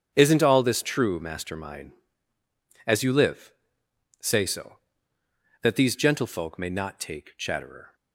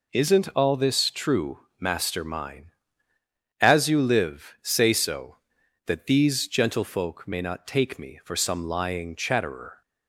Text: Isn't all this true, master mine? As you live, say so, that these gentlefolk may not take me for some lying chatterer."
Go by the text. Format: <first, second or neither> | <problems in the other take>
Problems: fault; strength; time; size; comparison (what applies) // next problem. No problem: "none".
second | starts louder than the rest; strong; until 1.1 s; 7.5 dB // skips "me for some lying"; at 7.3 s